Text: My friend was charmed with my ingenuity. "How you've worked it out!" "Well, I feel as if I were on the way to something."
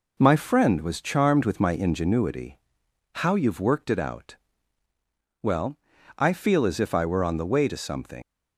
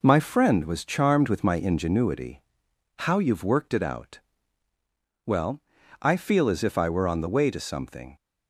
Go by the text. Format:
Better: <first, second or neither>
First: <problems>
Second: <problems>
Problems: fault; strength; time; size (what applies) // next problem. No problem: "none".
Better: second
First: leaves "something" unfinished; at 8.2 s; 100 ms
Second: none